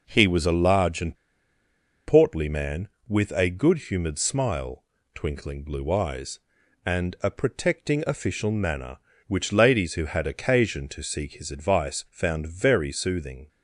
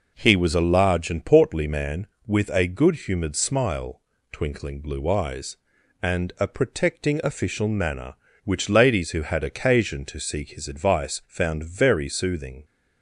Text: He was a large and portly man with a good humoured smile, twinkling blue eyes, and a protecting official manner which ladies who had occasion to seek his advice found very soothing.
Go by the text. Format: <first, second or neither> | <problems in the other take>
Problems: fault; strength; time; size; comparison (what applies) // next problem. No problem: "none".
second | pauses between "and" and "portly"; noticeable; at 1.1 s; 0.90 s long